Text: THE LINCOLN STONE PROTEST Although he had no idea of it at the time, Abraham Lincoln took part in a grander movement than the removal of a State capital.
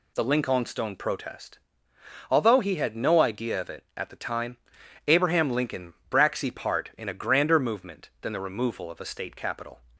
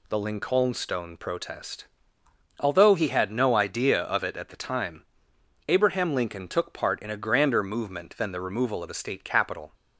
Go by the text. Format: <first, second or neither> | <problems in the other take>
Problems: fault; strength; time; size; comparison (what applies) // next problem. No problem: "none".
second | pauses between "PROTEST" and "Although"; noticeable; at 1.5 s; 0.72 s long; noticeable in the second // says "braxy" for "took"; at 6.1 s